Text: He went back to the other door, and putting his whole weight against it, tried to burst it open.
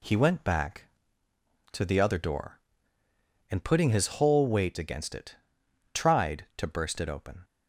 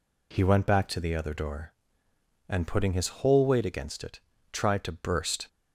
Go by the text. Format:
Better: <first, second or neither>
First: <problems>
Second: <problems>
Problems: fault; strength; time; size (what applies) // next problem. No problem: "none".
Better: first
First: none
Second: stops before "it open"; at 5.4 s